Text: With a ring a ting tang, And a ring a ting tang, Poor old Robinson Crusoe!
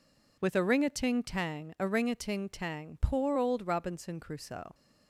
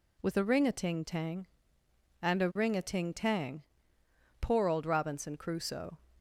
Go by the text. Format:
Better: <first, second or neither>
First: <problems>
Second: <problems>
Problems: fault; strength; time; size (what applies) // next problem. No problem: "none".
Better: second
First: skips "And"; at 1.7 s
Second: none